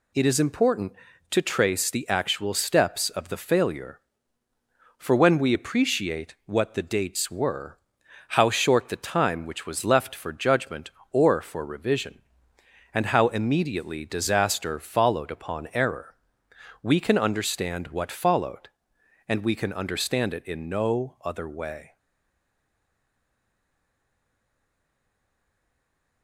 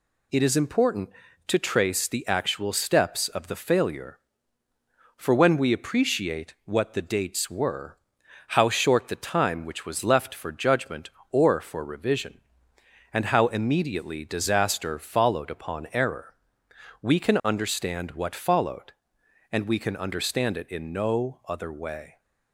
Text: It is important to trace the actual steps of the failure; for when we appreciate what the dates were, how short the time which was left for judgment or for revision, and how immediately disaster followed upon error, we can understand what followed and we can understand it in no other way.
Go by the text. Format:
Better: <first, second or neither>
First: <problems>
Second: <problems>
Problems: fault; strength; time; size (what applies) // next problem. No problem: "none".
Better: second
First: stays silent after the last word; strong; from 21.9 s on; 4.3 s long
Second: none